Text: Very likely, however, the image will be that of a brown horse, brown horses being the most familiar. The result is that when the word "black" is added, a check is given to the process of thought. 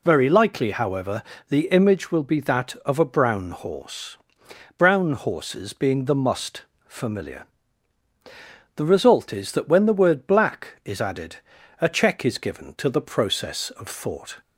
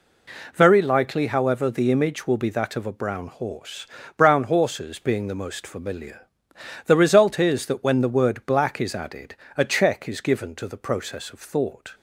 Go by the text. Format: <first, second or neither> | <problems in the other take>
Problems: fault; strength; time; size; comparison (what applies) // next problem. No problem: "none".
second | says "must" for "most"; at 6.1 s